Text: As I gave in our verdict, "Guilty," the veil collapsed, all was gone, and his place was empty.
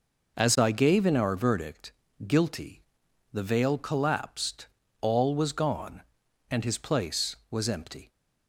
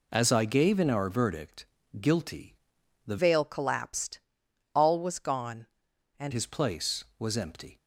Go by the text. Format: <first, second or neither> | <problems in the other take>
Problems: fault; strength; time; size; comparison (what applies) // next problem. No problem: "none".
first | changes voice from "veil" to "and"; from 3.1 to 6.3 s; 3.2 s long